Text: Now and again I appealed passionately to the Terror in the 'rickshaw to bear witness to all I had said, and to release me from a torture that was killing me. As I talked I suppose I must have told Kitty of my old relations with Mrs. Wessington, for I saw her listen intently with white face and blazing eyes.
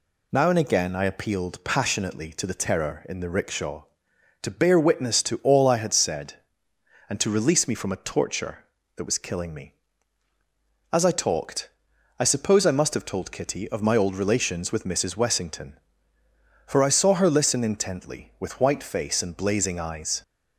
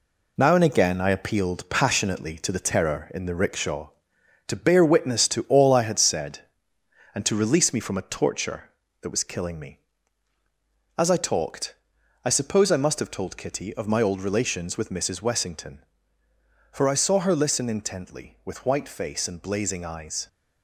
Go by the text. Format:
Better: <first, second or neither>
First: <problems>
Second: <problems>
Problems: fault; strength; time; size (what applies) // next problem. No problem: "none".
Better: first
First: pauses between "talked" and "I"; noticeable; at 11.6 s; 0.52 s long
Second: gets quieter; throughout; 7 dB // pauses between "talked" and "I"; noticeable; at 11.7 s; 0.52 s long